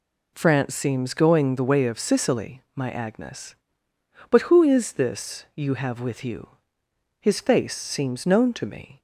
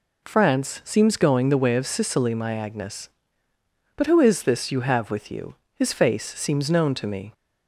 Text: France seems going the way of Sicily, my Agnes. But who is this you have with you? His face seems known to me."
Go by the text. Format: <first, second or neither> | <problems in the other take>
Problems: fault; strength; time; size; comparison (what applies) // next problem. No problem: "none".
neither | none